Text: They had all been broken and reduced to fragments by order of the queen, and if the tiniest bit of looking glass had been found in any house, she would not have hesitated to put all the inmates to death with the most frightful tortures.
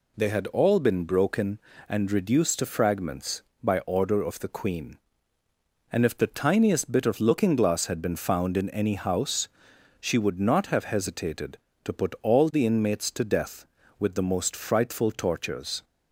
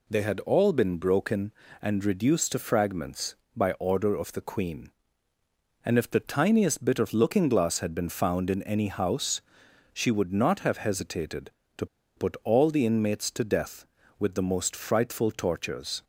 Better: first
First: none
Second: pauses between "to" and "put"; slight; at 11.8 s; 0.31 s long

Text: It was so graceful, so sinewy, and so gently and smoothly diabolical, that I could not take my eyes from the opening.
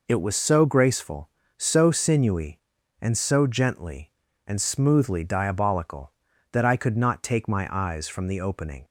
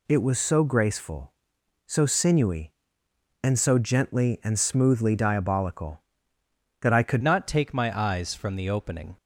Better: first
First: none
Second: changes voice at "not"; from 7.2 s on; 1.9 s long

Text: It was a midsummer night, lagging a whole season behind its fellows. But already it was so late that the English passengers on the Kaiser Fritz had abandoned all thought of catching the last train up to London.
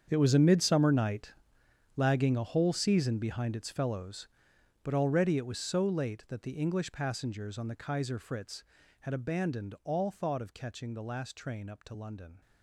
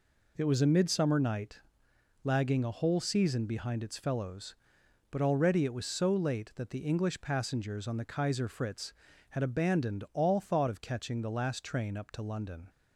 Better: second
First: gets quieter; strong; throughout; 16.5 dB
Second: none

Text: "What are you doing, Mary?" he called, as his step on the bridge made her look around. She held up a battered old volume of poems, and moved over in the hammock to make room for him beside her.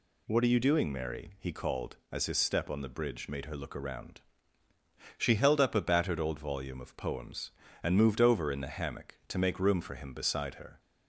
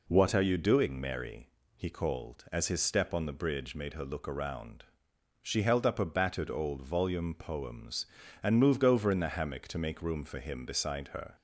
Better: first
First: none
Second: skips "of"; at 7.3 s

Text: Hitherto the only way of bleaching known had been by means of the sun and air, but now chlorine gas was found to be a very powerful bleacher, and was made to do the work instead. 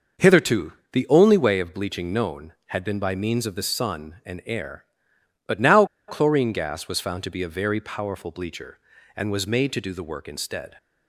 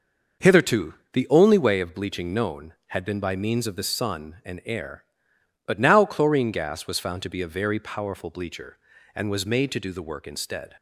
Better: second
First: pauses between "Hitherto" and "the"; slight; at 0.7 s; 0.20 s long // pauses between "now" and "chlorine"; slight; at 5.8 s; 0.23 s long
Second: pauses between "Hitherto" and "the"; slight; at 0.9 s; 0.19 s long

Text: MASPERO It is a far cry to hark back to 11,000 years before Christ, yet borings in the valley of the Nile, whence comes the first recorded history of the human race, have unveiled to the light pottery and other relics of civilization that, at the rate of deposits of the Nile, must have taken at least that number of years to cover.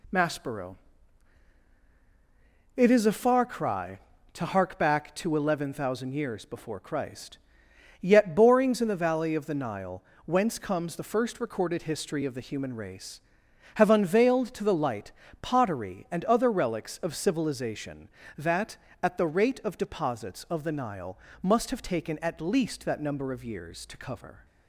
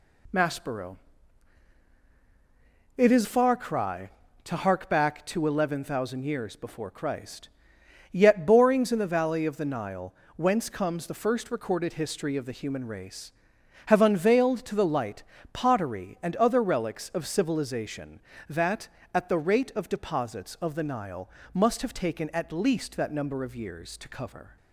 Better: first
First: pauses between "MASPERO" and "It"; strong; at 0.7 s; 2.0 s long // pauses between "light" and "pottery"; slight; at 15.1 s; 0.30 s long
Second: pauses between "MASPERO" and "It"; strong; at 0.9 s; 2.0 s long // skips "a"; at 3.2 s // pauses between "light" and "pottery"; slight; at 15.2 s; 0.30 s long

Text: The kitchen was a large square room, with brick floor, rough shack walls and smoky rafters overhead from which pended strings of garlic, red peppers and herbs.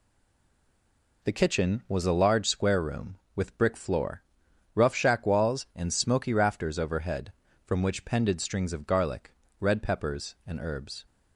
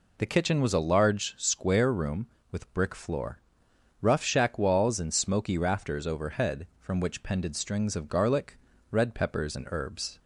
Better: second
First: stays silent before the first word; noticeable; until 1.2 s; 1.2 s long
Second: none

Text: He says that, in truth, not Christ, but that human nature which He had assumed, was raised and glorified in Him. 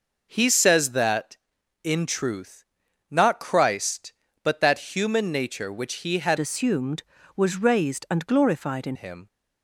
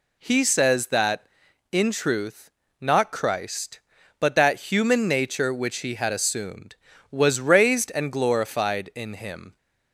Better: second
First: changes voice from "assumed" to "in"; from 6.3 to 8.9 s; 2.6 s long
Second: none

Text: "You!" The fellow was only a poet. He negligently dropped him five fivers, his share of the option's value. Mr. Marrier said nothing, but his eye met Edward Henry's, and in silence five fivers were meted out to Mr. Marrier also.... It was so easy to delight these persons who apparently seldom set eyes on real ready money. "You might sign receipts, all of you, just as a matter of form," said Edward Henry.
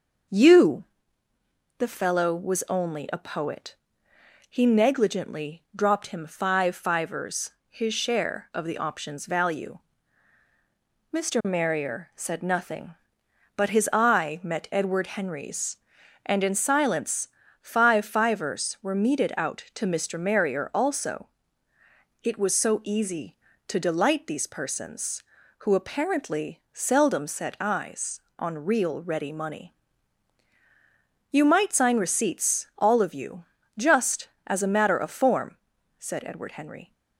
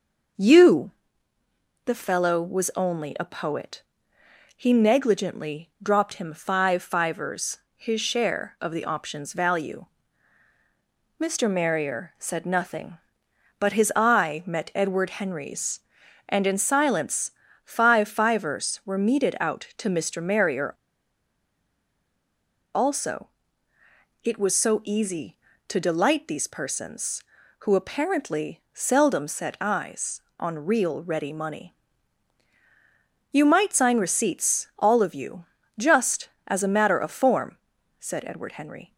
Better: first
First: starts louder than the rest; noticeable; until 2.2 s; 6 dB // pauses between "silence" and "five"; slight; at 17.2 s; 0.32 s long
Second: starts louder than the rest; noticeable; until 2.3 s; 6 dB // pauses between "silence" and "five"; slight; at 17.3 s; 0.32 s long // pauses between "Marrier" and "also"; strong; at 20.7 s; 2.0 s long

